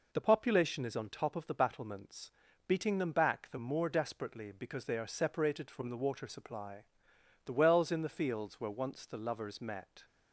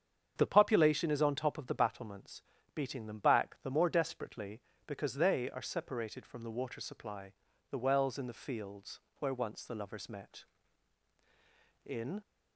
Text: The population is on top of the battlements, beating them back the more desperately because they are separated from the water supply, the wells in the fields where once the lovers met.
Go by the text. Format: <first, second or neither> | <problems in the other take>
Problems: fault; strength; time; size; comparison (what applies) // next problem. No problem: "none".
first | starts louder than the rest; strong; until 1.3 s; 8 dB // pauses between "fields" and "where"; slight; at 8.9 s; 0.20 s long // goes on to say "In"; slight; from 11.8 s on; 0.36 s long